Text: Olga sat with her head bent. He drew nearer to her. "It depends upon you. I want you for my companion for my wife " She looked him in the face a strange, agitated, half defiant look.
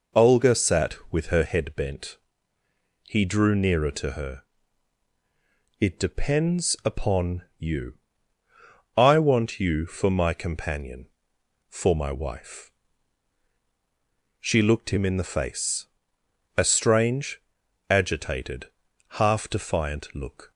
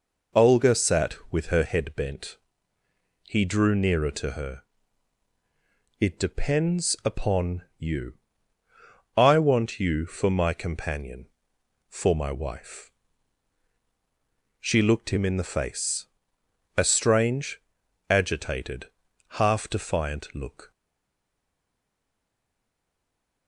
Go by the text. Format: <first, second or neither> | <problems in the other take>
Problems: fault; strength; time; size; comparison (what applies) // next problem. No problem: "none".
first | pauses between "face" and "a"; noticeable; at 16.0 s; 0.72 s long; noticeable in the first // stays silent after the last word; strong; from 20.7 s on; 2.7 s long